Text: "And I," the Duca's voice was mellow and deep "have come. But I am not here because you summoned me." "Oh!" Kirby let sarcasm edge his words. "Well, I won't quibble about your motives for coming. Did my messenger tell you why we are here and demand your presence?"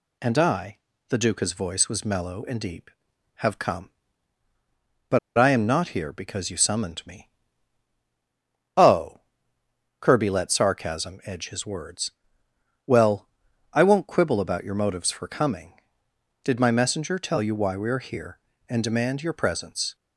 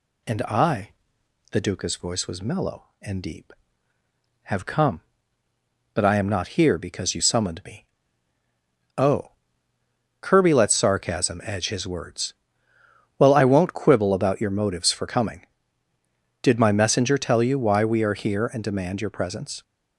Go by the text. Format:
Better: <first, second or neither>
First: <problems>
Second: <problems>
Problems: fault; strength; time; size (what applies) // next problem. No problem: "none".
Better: second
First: pauses between "But" and "I"; slight; at 5.1 s; 0.18 s long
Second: none